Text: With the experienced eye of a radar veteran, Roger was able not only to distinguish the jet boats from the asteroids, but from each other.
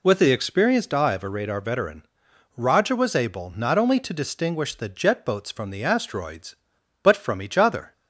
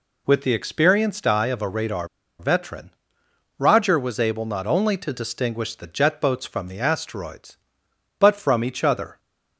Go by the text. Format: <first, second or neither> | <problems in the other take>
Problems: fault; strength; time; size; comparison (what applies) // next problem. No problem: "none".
first | pauses between "radar" and "veteran"; slight; at 2.0 s; 0.32 s long